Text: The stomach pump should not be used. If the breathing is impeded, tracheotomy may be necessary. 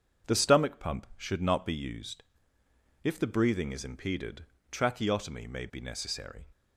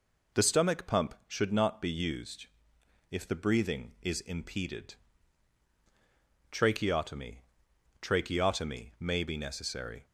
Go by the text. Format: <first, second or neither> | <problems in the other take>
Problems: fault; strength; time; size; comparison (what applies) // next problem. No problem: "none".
first | says "tracheotomy" twice; at 8.0 s